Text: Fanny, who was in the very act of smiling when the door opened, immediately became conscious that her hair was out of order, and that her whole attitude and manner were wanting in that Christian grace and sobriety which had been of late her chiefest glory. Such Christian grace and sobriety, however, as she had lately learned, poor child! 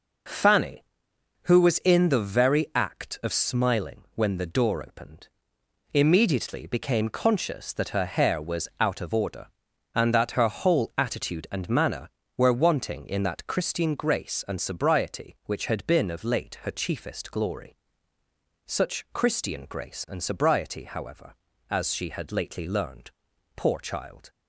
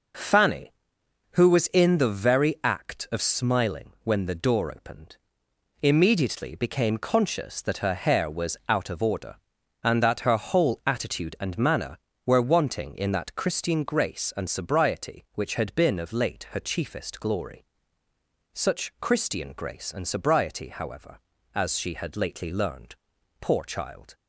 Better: neither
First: none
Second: none

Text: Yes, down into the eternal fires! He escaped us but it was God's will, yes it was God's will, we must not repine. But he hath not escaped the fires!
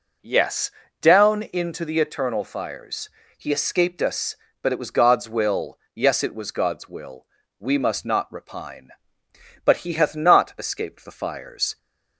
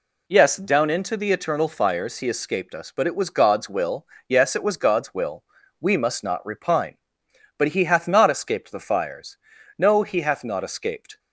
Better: first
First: none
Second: goes on to say "No he hath not escaped"; from 9.7 s on; 1.4 s long

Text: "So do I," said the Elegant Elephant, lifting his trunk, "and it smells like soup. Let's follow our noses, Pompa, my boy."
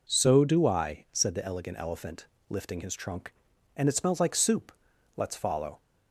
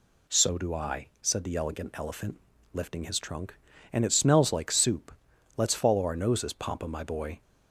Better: second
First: stops before "our noses Pompa my boy"; at 5.7 s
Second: none

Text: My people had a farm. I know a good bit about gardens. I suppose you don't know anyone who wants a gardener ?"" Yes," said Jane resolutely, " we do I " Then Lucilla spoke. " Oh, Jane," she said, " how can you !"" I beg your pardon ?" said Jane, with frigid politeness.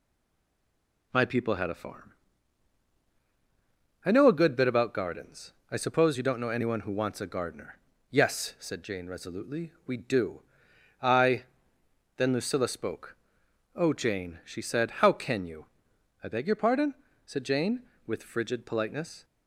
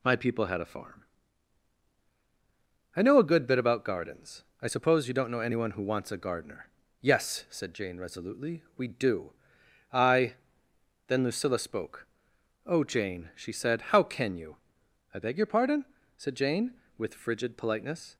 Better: second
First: stays silent before the first word; until 1.1 s; 1.1 s long // pauses between "do" and "I"; noticeable; at 10.4 s; 0.58 s long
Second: pauses between "do" and "I"; noticeable; at 9.3 s; 0.58 s long

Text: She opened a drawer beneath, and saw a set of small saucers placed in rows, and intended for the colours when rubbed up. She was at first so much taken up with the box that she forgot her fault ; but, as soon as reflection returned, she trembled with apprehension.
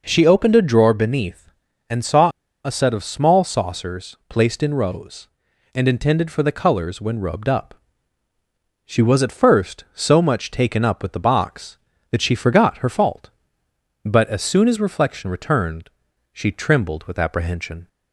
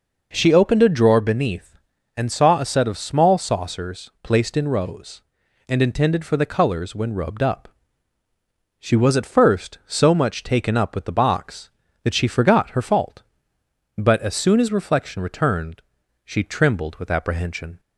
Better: second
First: pauses between "saw" and "a"; slight; at 2.3 s; 0.34 s long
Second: none

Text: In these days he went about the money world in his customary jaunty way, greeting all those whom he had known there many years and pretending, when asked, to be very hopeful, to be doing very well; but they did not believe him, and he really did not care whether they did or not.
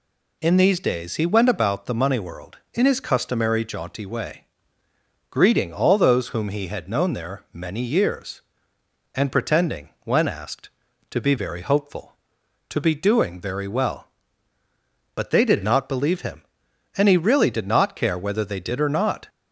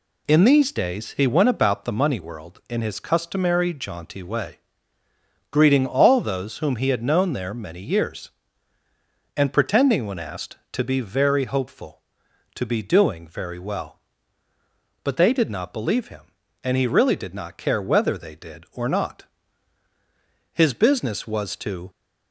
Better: first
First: none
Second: goes on to say "His business was to"; from 20.5 s on; 1.3 s long

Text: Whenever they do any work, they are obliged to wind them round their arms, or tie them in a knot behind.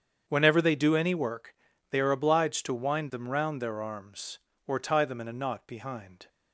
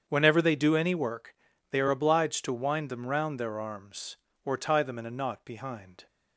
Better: neither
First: starts louder than the rest; strong; until 1.2 s; 7.5 dB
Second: starts louder than the rest; strong; until 1.0 s; 7.5 dB

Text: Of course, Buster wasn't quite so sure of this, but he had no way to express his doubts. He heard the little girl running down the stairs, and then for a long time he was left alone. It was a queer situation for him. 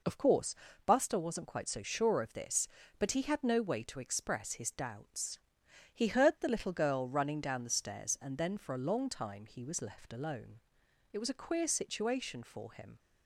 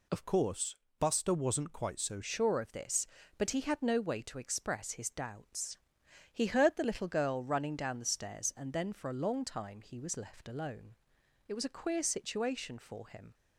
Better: first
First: none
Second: changes voice from "course" to "so"; from 0.2 to 2.2 s; 2.0 s long

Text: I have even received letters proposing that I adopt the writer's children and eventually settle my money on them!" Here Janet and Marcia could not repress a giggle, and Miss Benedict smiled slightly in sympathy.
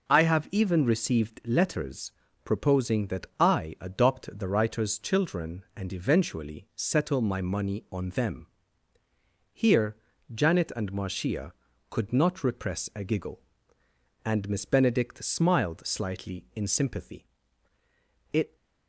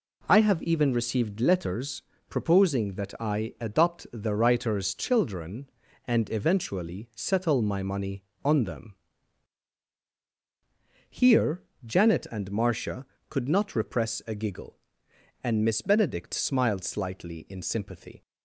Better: second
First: pauses between "letters" and "proposing"; slight; at 2.1 s; 0.32 s long // pauses between "Here" and "Janet"; at 9.9 s; 0.38 s long // goes on to say "It"; slight; from 18.3 s on; 0.24 s long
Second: pauses between "letters" and "proposing"; slight; at 2.0 s; 0.26 s long // pauses between "Here" and "Janet"; slight; at 11.6 s; 0.22 s long

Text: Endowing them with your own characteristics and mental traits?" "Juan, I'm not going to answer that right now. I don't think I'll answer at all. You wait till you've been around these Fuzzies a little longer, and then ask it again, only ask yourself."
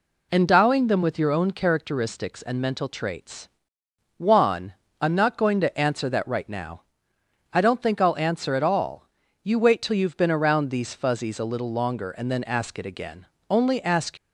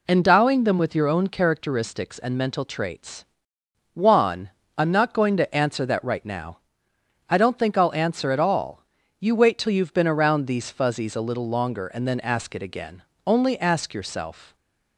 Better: second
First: stops before "yourself"; at 14.1 s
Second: none

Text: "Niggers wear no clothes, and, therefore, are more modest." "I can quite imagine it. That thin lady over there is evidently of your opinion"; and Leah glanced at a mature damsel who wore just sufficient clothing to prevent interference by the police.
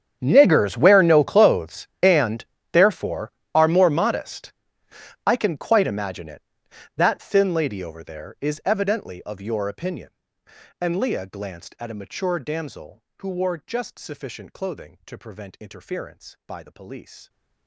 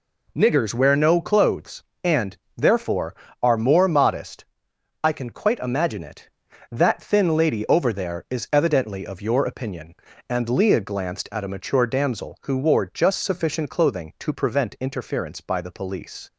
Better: second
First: gets quieter; strong; throughout; 21.5 dB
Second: none

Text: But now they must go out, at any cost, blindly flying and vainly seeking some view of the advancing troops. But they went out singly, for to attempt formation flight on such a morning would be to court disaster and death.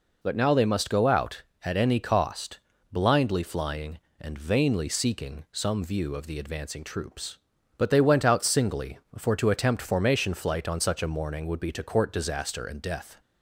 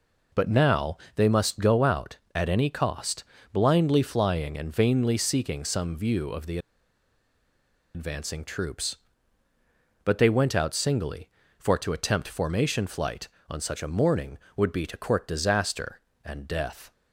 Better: first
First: none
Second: pauses between "now" and "they"; slight; at 0.9 s; 0.20 s long // pauses between "the" and "advancing"; strong; at 6.5 s; 1.3 s long

